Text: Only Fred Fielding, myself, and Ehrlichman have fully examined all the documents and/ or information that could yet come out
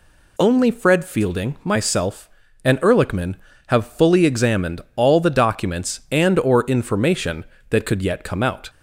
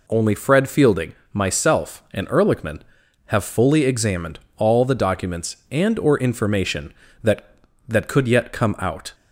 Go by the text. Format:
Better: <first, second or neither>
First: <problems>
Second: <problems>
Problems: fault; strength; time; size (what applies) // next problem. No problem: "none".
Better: first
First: none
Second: pauses between "examined" and "all"; slight; at 4.3 s; 0.18 s long // says "that" twice; at 7.8 s